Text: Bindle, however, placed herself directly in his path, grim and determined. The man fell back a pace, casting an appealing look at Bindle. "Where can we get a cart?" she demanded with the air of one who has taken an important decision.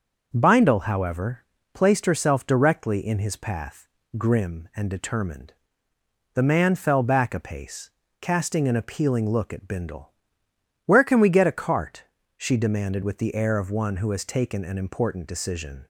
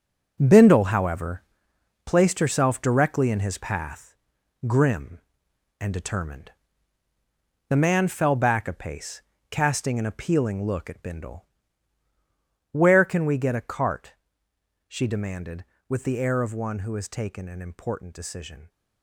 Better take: first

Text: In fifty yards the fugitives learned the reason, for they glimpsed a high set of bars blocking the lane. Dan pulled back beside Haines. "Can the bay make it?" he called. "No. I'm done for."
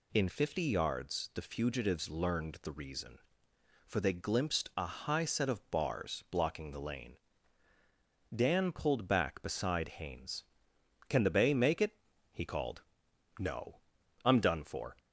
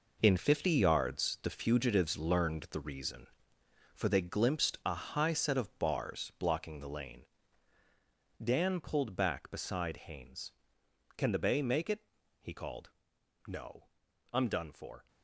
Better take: first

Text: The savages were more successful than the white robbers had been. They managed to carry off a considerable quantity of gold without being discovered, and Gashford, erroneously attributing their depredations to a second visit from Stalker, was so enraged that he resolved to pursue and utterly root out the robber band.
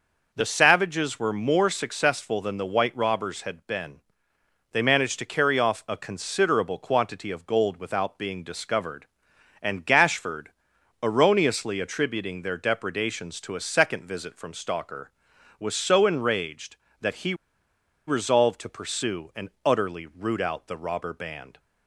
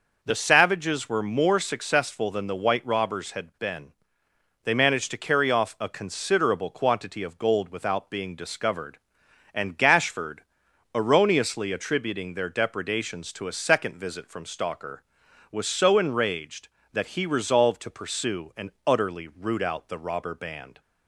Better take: second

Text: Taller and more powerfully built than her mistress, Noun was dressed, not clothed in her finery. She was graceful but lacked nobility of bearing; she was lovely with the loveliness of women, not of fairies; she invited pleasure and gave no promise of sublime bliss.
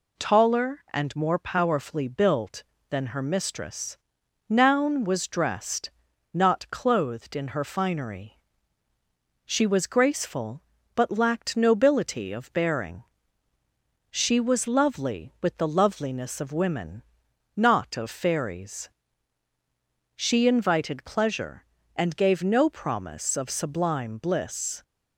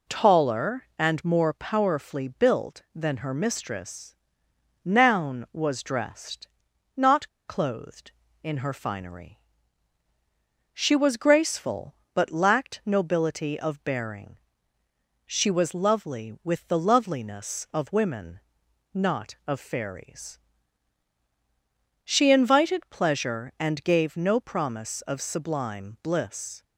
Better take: first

